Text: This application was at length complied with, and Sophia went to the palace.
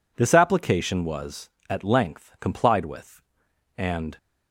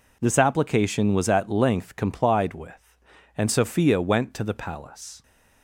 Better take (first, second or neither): second